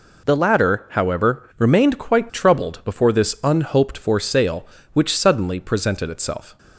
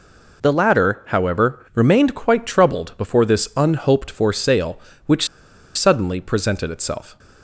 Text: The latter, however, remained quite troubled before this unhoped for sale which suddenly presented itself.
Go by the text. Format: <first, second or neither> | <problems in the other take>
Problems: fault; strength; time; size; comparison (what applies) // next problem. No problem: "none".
first | pauses between "which" and "suddenly"; noticeable; at 5.2 s; 0.49 s long